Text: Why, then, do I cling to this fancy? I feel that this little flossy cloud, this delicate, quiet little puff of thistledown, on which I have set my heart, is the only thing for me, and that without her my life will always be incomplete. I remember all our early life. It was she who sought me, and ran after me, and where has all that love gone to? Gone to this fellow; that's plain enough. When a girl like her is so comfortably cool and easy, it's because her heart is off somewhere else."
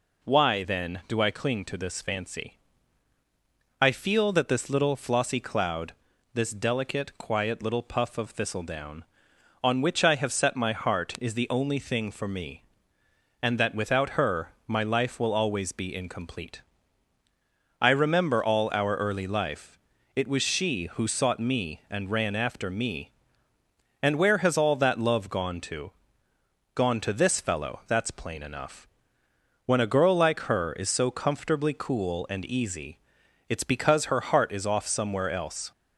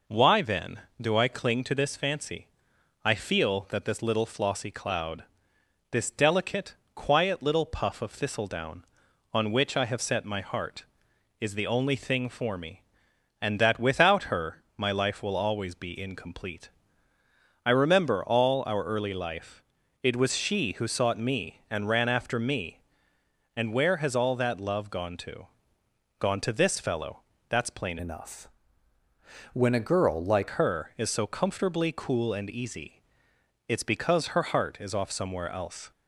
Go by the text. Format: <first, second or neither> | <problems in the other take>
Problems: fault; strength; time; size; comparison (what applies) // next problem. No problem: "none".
first | pauses between "her" and "my"; slight; at 14.6 s; 0.16 s long; slight in the first // changes voice from "enough" to "like"; from 27.9 to 30.4 s; 2.5 s long